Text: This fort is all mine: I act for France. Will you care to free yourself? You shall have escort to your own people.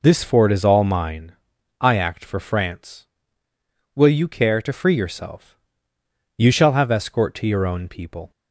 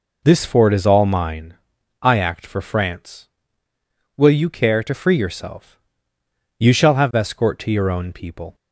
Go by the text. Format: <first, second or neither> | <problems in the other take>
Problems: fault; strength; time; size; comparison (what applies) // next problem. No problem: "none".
neither | none